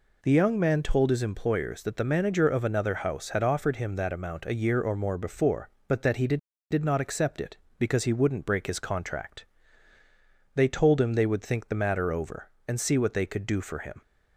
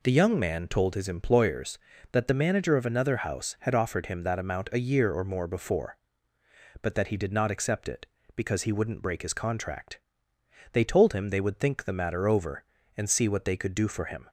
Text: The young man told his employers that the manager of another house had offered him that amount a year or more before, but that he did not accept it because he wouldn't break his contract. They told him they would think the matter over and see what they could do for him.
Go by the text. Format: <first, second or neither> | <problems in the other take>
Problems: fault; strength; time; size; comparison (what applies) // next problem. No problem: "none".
second | says "did" twice; at 6.6 s